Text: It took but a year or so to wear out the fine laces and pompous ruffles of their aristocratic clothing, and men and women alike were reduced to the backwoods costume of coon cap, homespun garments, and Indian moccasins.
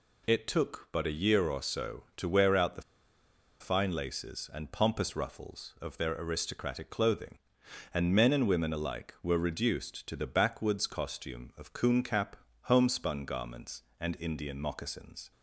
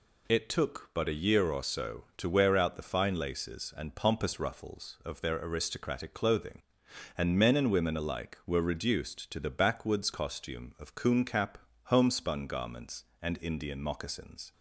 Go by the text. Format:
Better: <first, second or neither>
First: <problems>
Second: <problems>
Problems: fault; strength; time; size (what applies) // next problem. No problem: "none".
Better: second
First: pauses between "the" and "fine"; noticeable; at 2.8 s; 0.78 s long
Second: none